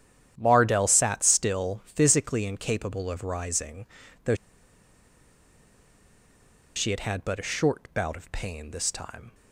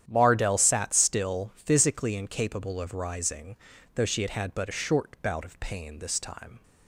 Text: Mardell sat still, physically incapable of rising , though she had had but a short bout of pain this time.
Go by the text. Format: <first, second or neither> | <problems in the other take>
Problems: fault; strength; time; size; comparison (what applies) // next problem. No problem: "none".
second | starts louder than the rest; strong; until 1.4 s; 10 dB; strong in the second // pauses between "though" and "she"; strong; at 4.3 s; 2.4 s long